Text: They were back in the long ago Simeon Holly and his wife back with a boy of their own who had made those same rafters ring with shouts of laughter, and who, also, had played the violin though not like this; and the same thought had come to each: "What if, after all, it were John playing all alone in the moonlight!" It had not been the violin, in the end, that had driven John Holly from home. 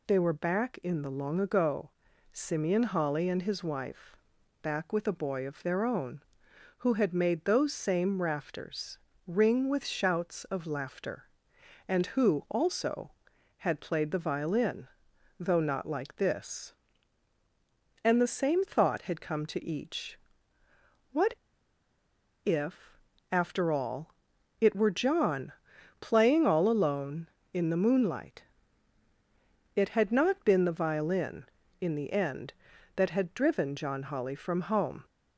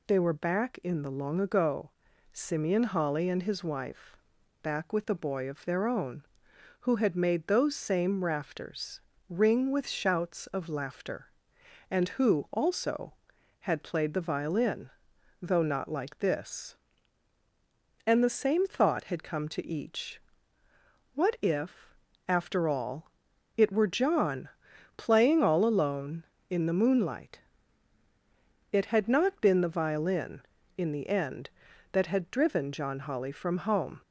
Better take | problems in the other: second | pauses between "ago" and "Simeon"; at 1.8 s; 0.42 s long; also in the second // pauses between "wife" and "back"; noticeable; at 4.1 s; 0.46 s long; noticeable in the second // pauses between "rafters" and "ring"; slight; at 8.9 s; 0.26 s long; slight in the second // pauses between "violin" and "though"; noticeable; at 14.8 s; 0.52 s long; noticeable in the second // pauses between "What" and "if"; at 21.3 s; 1.1 s long // pauses between "John" and "playing"; noticeable; at 25.5 s; 0.48 s long; noticeable in the second

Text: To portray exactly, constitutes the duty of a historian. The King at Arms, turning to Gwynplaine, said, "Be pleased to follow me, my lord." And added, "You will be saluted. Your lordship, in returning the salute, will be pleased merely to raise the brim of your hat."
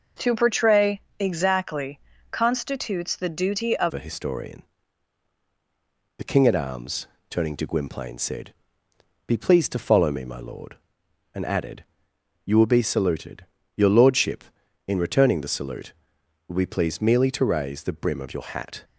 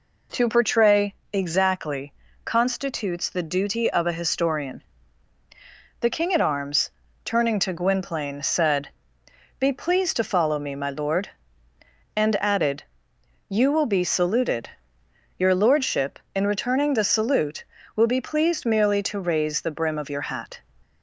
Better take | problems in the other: second | pauses between "portray" and "exactly"; slight; at 0.9 s; 0.20 s long; slight in the second // changes voice at "a"; from 3.9 s on; 14.9 s long

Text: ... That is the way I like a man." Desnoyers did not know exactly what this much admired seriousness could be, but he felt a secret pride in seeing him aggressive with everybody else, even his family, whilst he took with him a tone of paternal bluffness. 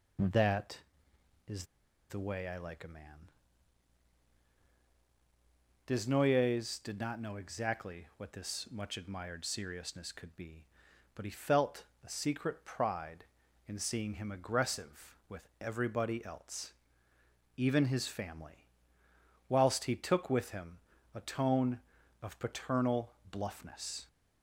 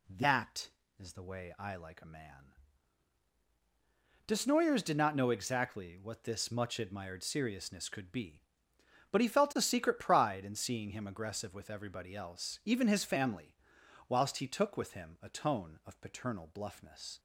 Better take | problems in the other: second | pauses between "is" and "the"; at 1.6 s; 0.45 s long // pauses between "felt" and "a"; slight; at 11.8 s; 0.18 s long // pauses between "him" and "a"; slight; at 20.7 s; 0.34 s long // pauses between "paternal" and "bluffness"; slight; at 23.1 s; 0.18 s long

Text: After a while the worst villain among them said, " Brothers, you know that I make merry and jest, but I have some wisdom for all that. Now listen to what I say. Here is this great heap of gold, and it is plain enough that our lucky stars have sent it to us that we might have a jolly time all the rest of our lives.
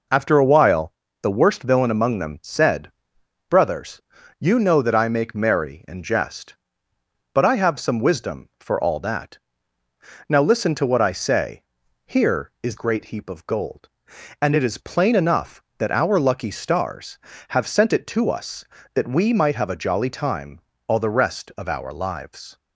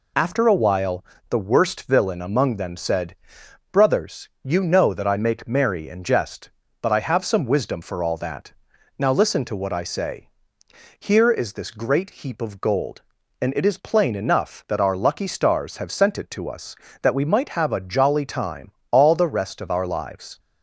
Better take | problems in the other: second | pauses between "while" and "the"; slight; at 0.9 s; 0.26 s long; slight in the second // skips "this"; at 12.7 s // pauses between "time" and "all"; slight; at 20.5 s; 0.30 s long; slight in the second

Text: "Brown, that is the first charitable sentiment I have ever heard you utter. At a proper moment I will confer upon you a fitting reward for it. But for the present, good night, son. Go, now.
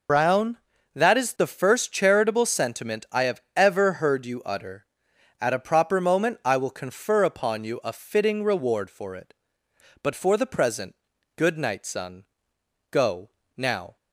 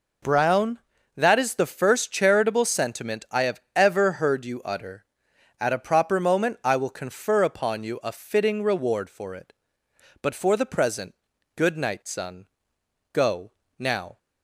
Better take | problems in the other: second | loses the start of "Brown"; at 0.0 s; 90 ms // pauses between "have" and "ever"; slight; at 3.3 s; 0.16 s long; slight in the second

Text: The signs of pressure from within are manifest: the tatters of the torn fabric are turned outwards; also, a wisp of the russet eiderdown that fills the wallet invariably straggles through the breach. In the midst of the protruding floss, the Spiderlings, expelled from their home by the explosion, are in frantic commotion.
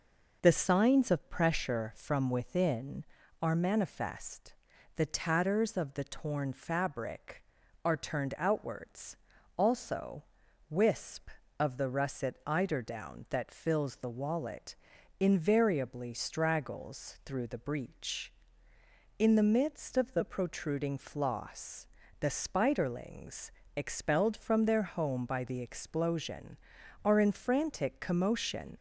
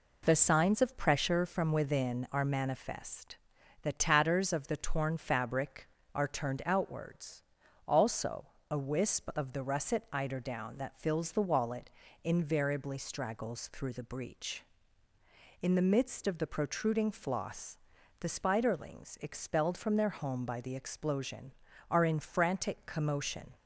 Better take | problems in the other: second | skips "a"; at 10.4 s // pauses between "wallet" and "invariably"; at 14.7 s; 0.44 s long; slight in the second

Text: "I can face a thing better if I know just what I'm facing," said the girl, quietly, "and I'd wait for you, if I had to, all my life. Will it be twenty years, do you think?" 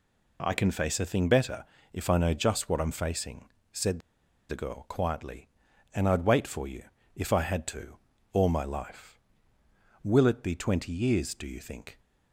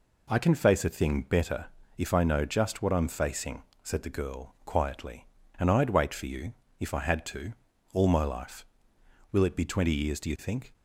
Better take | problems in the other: second | pauses between "better" and "if"; slight; at 1.6 s; 0.28 s long; slight in the second // pauses between "said" and "the"; noticeable; at 3.9 s; 0.50 s long

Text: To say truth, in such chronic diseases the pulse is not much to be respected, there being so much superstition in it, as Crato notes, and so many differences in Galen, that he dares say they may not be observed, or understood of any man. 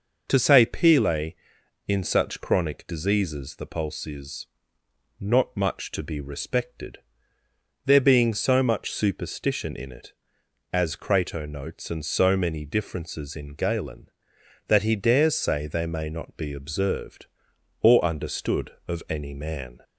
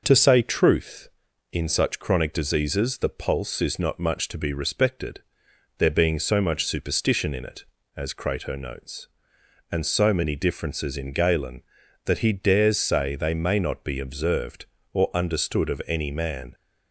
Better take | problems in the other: second | says "pele" for "truth"; at 0.6 s // pauses between "is" and "not"; noticeable; at 4.4 s; 0.72 s long

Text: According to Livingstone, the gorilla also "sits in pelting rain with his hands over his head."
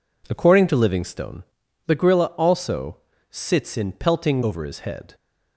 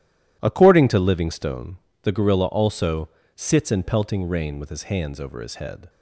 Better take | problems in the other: second | pauses between "also" and "sits"; slight; at 2.9 s; 0.32 s long; slight in the second // skips "rain with his hands"; at 4.4 s

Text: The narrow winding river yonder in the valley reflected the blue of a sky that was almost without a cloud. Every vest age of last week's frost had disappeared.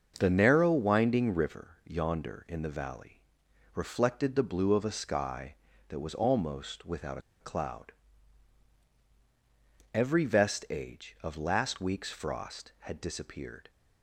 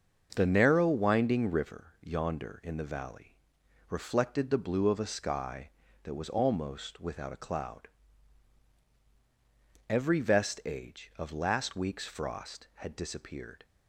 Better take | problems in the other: second | starts louder than the rest; until 1.2 s; 6.5 dB; also in the second // pauses between "valley" and "reflected"; noticeable; at 3.2 s; 0.54 s long; noticeable in the second // pauses between "without" and "a"; slight; at 7.1 s; 0.21 s long

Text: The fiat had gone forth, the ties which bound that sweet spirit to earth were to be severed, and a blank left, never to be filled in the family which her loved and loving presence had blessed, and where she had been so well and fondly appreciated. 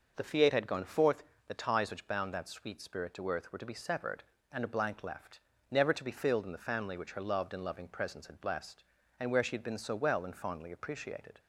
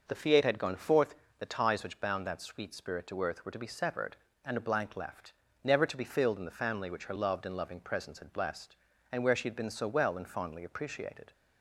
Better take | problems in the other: neither | none

